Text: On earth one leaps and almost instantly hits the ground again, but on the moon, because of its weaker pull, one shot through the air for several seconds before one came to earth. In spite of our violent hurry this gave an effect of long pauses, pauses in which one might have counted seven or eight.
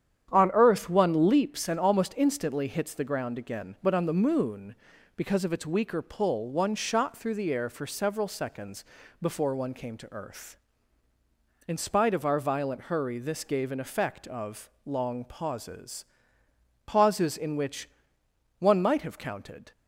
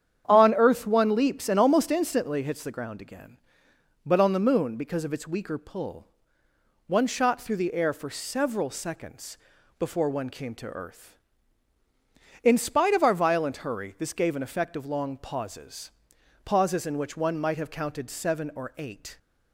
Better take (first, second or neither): second